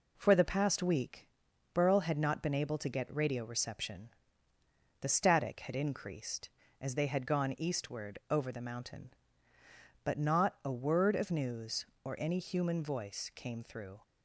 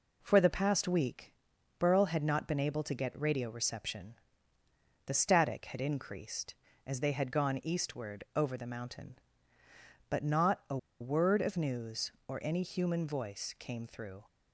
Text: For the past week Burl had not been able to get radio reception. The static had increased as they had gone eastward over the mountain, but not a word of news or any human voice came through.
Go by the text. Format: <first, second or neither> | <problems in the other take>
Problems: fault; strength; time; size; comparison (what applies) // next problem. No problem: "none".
first | pauses between "week" and "Burl"; at 1.3 s; 0.44 s long; also in the first // pauses between "a" and "word"; slight; at 10.7 s; 0.22 s long